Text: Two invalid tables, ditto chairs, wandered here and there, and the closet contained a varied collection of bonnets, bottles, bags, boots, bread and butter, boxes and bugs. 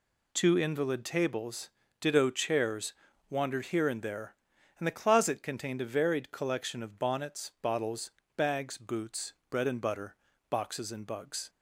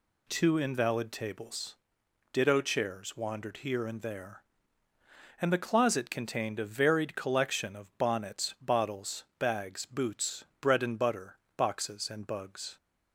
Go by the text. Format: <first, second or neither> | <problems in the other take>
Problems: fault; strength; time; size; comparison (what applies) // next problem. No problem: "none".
neither | none